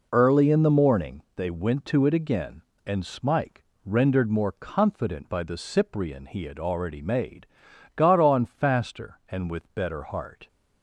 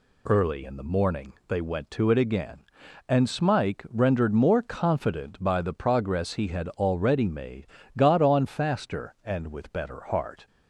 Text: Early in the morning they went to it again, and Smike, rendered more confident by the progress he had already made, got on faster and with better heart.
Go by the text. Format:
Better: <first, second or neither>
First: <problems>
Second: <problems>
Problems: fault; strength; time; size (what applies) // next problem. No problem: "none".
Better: second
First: says "cyprian" for "progress"; at 5.5 s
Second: none